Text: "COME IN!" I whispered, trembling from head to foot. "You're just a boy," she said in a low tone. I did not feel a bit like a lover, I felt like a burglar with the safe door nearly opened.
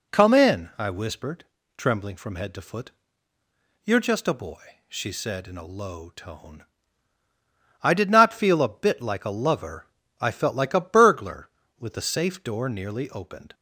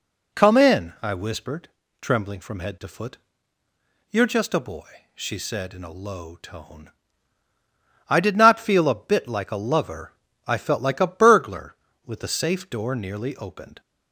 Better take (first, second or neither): neither